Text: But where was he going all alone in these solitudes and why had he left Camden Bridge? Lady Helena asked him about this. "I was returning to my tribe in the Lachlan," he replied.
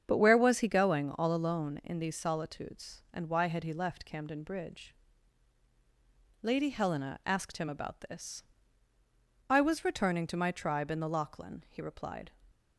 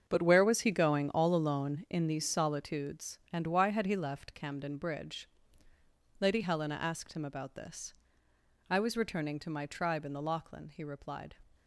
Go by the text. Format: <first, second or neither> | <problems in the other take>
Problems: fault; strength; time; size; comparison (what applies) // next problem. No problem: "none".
first | gets quieter; strong; throughout; 11.5 dB // starts louder than the rest; strong; until 1.0 s; 7 dB; strong in the first